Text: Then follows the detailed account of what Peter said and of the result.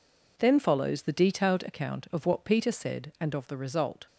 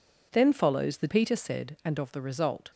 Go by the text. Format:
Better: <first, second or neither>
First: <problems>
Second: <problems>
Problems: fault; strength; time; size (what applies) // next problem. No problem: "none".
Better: first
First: none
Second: skips "detailed account of what"; at 1.0 s